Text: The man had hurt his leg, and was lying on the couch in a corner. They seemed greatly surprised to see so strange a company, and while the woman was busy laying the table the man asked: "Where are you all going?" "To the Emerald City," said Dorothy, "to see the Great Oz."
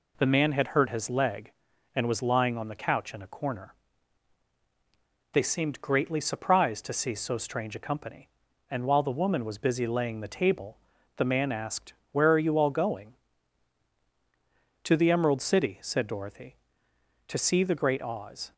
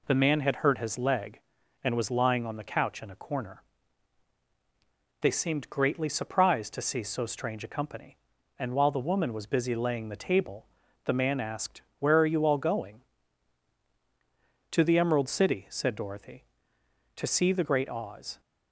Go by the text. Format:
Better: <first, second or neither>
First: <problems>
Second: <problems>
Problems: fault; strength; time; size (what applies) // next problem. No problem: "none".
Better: neither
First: pauses between "table" and "the"; at 10.7 s; 0.38 s long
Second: pauses between "table" and "the"; at 10.6 s; 0.38 s long